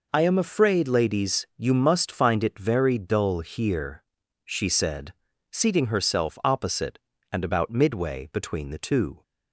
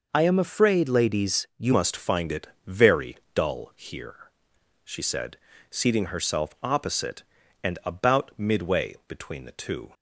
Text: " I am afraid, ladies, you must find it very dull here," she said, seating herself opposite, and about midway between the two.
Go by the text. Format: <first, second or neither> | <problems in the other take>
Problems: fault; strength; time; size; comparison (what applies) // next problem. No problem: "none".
first | changes voice at "must"; from 1.7 s on; 8.2 s long // pauses between "it" and "very"; slight; at 2.4 s; 0.18 s long // pauses between "very" and "dull"; slight; at 3.1 s; 0.18 s long